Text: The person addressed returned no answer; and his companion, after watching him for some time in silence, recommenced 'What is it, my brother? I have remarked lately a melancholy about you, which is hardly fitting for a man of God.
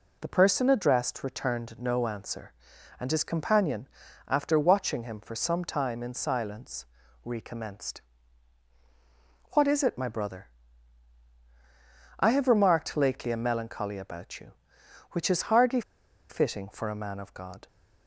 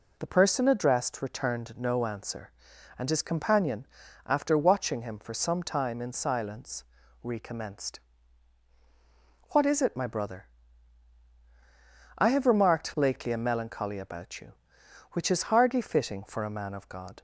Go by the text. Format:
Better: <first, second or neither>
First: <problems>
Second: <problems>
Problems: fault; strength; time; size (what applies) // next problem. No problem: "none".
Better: second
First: pauses between "recommenced" and "What"; strong; at 8.0 s; 1.5 s long // pauses between "hardly" and "fitting"; noticeable; at 15.8 s; 0.48 s long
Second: pauses between "recommenced" and "What"; strong; at 7.9 s; 1.5 s long